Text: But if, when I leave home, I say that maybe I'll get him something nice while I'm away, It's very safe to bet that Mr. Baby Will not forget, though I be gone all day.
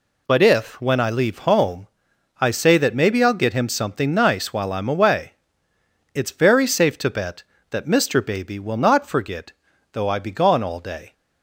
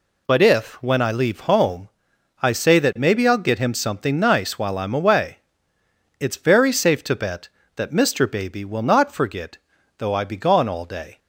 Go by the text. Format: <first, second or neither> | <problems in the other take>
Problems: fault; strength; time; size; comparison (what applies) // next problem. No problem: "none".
neither | none